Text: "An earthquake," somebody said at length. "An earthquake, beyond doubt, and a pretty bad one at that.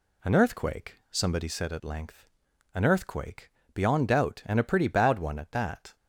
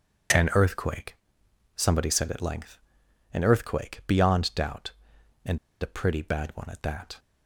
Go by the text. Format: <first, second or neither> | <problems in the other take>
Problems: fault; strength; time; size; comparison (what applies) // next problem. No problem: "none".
first | pauses between "and" and "a"; slight; at 5.5 s; 0.23 s long